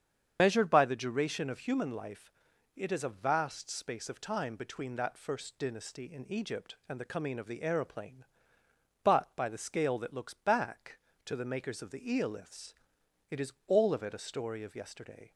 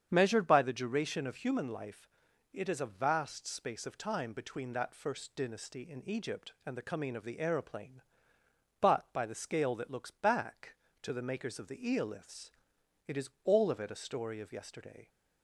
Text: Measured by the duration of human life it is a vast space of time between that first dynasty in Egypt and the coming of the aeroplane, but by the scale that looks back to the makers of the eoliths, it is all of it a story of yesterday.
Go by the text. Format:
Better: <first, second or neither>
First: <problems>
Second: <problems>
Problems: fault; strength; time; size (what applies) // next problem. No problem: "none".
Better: second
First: loses the start of "Measured"; at 0.3 s; 65 ms // starts louder than the rest; strong; until 1.4 s; 7.5 dB // pauses between "life" and "it"; at 2.3 s; 0.42 s long // pauses between "is" and "all"; slight; at 13.5 s; 0.16 s long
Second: starts louder than the rest; strong; until 1.1 s; 8 dB // pauses between "life" and "it"; at 2.0 s; 0.42 s long // pauses between "is" and "all"; slight; at 13.2 s; 0.16 s long